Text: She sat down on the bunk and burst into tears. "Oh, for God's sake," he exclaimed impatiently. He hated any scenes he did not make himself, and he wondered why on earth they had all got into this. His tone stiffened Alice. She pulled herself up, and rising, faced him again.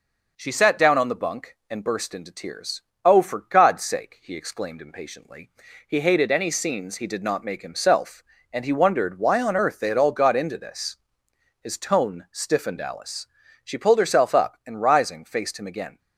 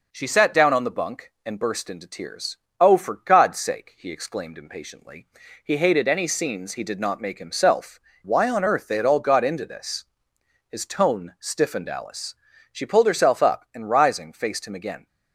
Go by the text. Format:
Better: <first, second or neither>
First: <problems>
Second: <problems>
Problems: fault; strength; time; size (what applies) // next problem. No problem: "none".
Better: first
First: none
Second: skips "and he wondered"; at 8.1 s